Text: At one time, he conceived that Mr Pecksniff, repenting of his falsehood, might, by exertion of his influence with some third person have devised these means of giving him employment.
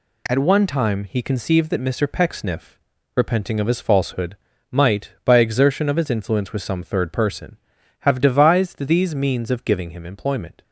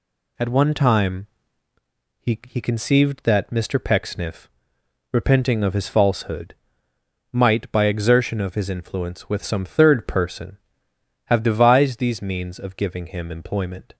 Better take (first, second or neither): first